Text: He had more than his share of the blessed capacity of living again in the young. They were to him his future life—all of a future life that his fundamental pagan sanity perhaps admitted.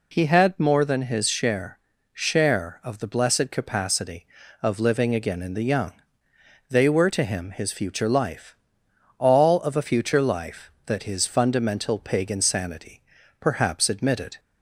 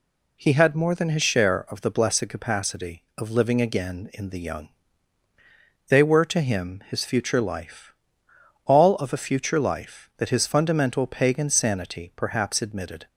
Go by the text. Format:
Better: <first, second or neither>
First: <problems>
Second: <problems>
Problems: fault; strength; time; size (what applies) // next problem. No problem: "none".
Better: second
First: says "share" twice; at 2.1 s // pauses between "sanity" and "perhaps"; slight; at 13.0 s; 0.36 s long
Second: none